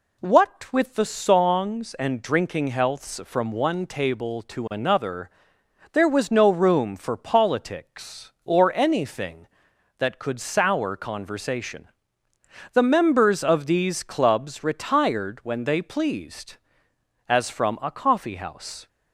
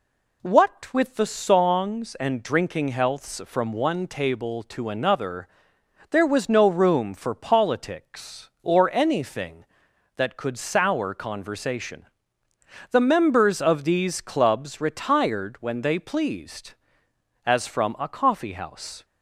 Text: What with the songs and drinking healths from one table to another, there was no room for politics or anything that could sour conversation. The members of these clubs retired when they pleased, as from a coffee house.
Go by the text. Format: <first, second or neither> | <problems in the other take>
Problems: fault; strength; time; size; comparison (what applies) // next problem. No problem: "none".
neither | none